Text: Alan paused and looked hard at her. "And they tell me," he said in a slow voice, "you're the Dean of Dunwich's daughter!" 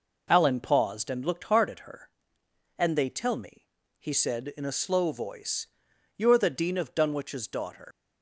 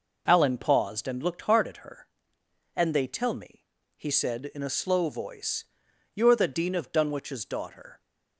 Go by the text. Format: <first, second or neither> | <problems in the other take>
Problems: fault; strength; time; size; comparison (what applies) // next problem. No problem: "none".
second | leaves "daughter" unfinished; at 7.9 s; 120 ms